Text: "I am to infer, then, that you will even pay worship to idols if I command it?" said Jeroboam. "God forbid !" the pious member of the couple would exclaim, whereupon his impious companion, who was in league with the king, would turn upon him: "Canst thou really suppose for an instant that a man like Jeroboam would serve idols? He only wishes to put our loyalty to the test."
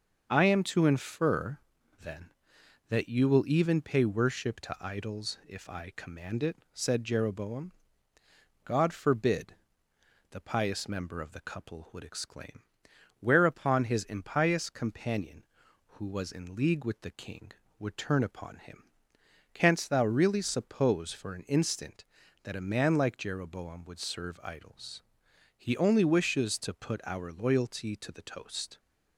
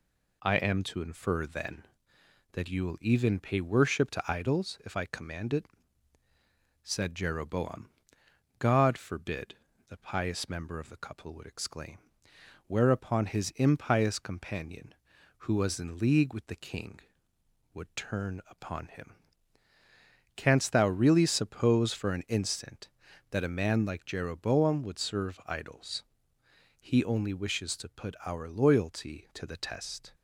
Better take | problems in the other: second | starts louder than the rest; until 1.2 s; 6.5 dB // says "toast" for "test"; at 28.2 s

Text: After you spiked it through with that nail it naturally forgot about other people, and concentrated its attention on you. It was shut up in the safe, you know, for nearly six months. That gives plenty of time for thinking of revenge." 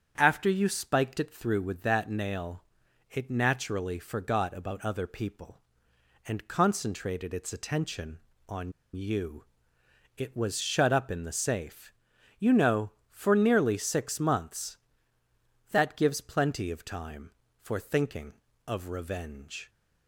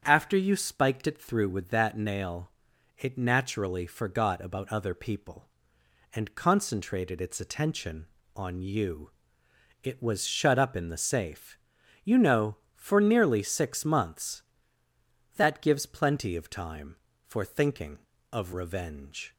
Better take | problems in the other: second | starts louder than the rest; strong; until 1.1 s; 8 dB; strong in the second // pauses between "nail" and "it"; noticeable; at 2.6 s; 0.48 s long; noticeable in the second // pauses between "on" and "you"; slight; at 8.7 s; 0.23 s long

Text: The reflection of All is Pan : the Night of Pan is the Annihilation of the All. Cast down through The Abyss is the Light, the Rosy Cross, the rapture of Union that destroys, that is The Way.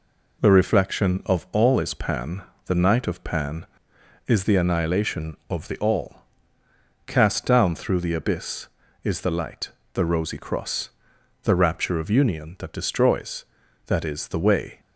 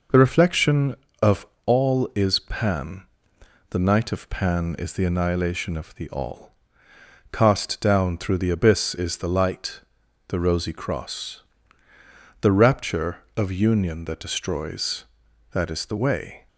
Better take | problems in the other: first | loses the start of "The"; at 0.0 s; 35 ms // pauses between "of" and "All"; slight; at 1.4 s; 0.20 s long

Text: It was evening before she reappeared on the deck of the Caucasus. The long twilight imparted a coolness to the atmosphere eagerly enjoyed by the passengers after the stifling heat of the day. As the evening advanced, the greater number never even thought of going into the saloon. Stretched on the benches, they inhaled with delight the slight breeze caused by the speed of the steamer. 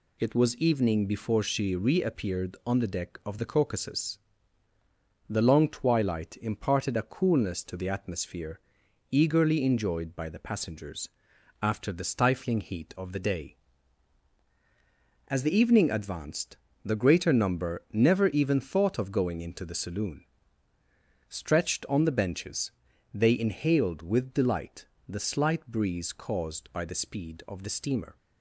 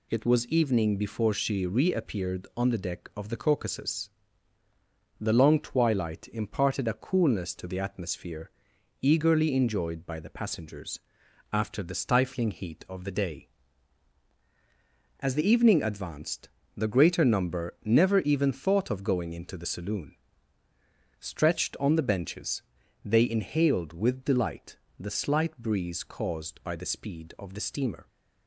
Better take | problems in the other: neither | pauses between "atmosphere" and "eagerly"; noticeable; the same in both // pauses between "passengers" and "after"; noticeable; the same in both // pauses between "delight" and "the"; slight; the same in both

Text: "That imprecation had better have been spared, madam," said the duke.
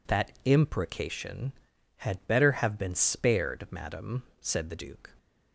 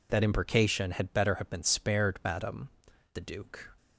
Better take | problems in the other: first | skips "said"; at 2.9 s

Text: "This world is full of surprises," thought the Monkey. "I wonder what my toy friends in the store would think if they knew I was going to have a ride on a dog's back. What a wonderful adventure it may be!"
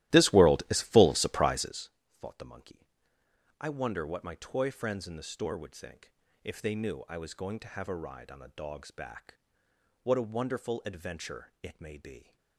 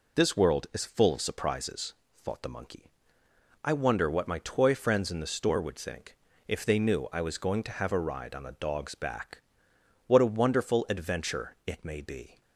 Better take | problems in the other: second | starts louder than the rest; strong; until 1.9 s; 15 dB // pauses between "think" and "if"; slight; at 6.1 s; 0.32 s long; slight in the second

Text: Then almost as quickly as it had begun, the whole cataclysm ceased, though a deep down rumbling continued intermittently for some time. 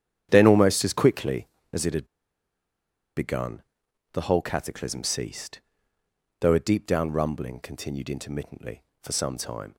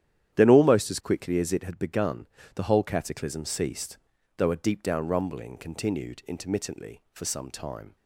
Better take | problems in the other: second | starts louder than the rest; strong; until 1.3 s; 10 dB; strong in the second // pauses between "had" and "begun"; at 2.0 s; 1.1 s long

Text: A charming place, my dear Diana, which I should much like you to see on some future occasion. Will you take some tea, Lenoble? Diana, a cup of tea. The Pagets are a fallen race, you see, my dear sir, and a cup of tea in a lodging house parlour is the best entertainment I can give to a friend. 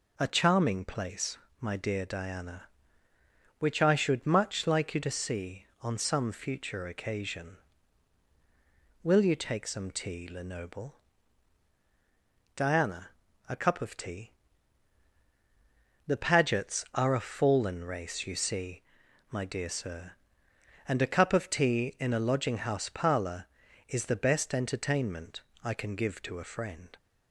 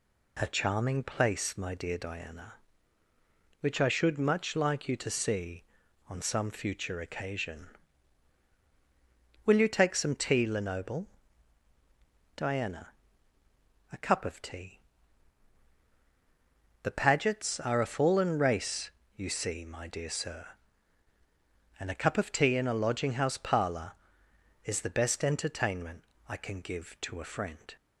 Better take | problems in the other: neither | pauses between "entertainment" and "I"; slight; the same in both

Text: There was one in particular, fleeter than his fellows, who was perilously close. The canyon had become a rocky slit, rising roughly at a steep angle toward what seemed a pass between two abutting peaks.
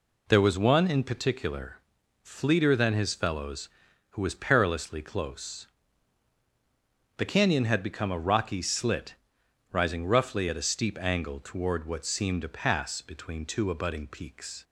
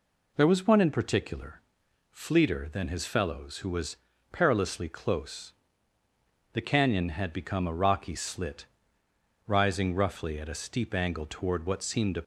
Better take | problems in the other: first | pauses between "was" and "perilously"; slight; at 3.9 s; 0.34 s long // stops before "pass between two abutting peaks"; at 12.2 s

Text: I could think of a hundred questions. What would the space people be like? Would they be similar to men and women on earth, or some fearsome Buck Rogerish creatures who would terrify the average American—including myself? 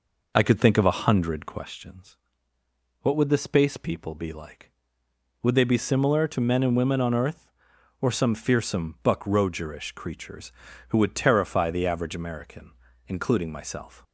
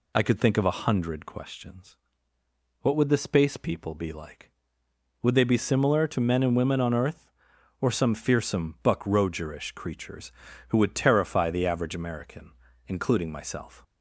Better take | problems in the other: second | starts louder than the rest; noticeable; until 1.8 s; 5 dB

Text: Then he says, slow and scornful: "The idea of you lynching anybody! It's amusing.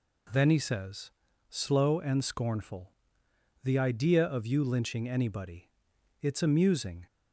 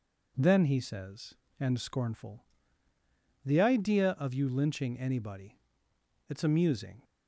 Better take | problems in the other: first | skips "slow"; at 1.4 s

